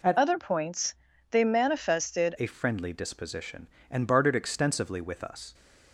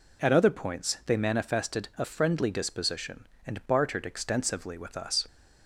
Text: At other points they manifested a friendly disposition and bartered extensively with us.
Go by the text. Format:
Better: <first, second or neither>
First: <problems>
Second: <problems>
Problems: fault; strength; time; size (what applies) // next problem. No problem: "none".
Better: second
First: changes voice from "other" to "manifested"; from 0.1 to 2.3 s; 2.2 s long // pauses between "points" and "they"; at 0.9 s; 0.38 s long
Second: none